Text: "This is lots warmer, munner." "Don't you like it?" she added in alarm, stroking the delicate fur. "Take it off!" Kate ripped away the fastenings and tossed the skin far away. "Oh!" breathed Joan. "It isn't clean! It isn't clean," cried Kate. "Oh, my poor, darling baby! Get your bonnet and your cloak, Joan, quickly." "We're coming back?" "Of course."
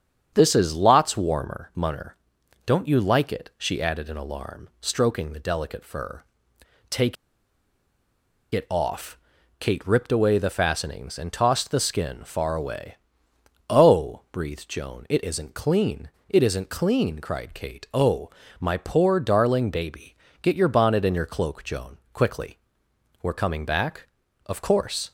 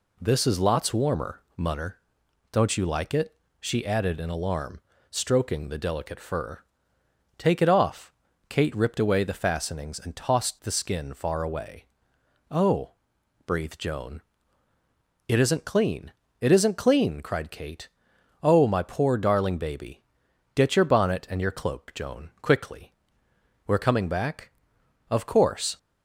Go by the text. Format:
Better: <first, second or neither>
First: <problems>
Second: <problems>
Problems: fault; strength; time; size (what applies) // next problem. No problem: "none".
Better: second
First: starts louder than the rest; strong; until 1.3 s; 7.5 dB // pauses between "Take" and "it"; strong; at 7.1 s; 1.3 s long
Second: none